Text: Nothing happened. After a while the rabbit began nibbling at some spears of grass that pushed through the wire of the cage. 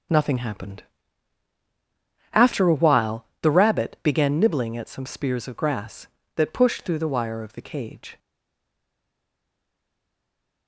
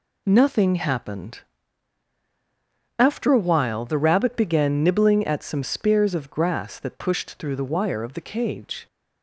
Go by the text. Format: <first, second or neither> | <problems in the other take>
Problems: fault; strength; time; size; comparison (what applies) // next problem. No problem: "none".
second | pauses between "while" and "the"; slight; at 3.2 s; 0.16 s long // stays silent after the last word; from 8.1 s on; 2.5 s long